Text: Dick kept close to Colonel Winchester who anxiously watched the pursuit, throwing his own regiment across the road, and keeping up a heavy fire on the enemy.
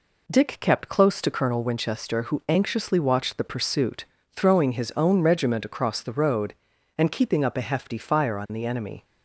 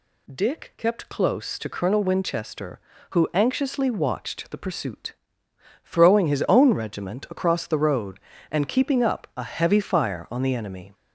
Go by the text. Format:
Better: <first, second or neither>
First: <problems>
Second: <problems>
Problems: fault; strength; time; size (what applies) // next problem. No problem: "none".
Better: second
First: says "hefty" for "heavy"; at 7.6 s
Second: none